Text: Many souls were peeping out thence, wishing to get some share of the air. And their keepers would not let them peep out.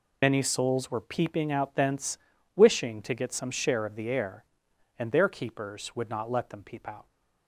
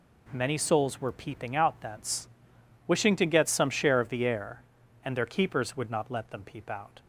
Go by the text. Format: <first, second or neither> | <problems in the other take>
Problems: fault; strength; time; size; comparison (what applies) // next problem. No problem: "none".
second | loses the start of "Many"; at 0.2 s; 45 ms